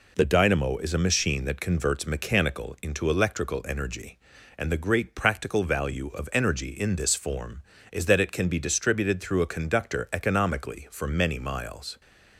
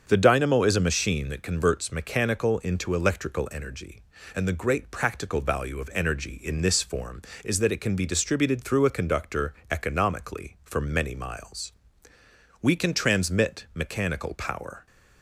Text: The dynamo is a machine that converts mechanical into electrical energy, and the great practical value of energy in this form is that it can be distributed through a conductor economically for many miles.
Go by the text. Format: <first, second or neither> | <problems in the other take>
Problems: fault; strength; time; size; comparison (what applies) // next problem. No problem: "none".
first | starts louder than the rest; until 1.0 s; 7 dB // pauses between "conductor" and "economically"; slight; at 9.5 s; 0.16 s long // goes on to say "We can transmit mechanical power"; strong; from 12.6 s on; 2.2 s long